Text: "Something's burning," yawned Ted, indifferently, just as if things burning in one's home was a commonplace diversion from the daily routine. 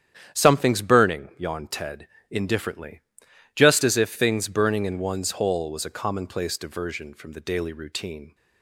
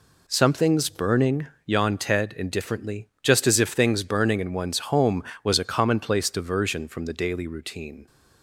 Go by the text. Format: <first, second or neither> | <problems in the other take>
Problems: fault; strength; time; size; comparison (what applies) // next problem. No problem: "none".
second | starts louder than the rest; strong; until 1.3 s; 9.5 dB // says "hole" for "home"; at 5.3 s